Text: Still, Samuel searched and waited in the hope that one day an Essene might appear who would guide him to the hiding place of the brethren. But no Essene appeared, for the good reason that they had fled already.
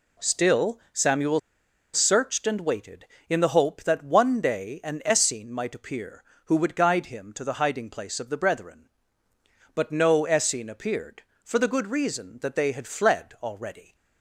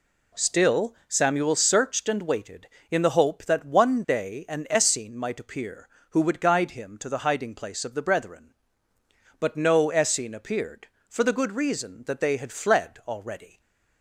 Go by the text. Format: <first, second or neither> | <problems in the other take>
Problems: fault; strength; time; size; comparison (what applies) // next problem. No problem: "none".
second | pauses between "Samuel" and "searched"; noticeable; at 1.3 s; 0.54 s long